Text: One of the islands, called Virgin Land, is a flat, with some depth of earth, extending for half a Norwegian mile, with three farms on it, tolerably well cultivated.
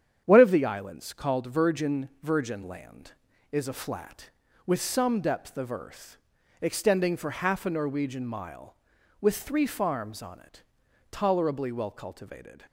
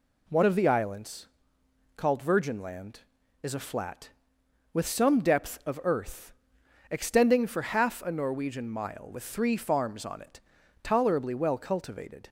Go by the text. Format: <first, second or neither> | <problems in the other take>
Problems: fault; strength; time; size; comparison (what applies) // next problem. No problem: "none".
second | starts louder than the rest; strong; until 1.2 s; 8.5 dB // says "Virgin" twice; at 2.2 s